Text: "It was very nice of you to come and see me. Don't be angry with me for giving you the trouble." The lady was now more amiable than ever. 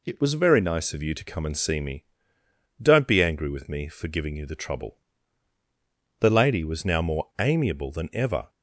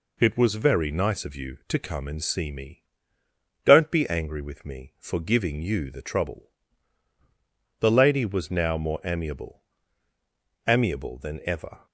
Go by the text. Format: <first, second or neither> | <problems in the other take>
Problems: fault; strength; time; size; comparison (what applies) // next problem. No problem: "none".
first | says "amiable" twice; at 10.6 s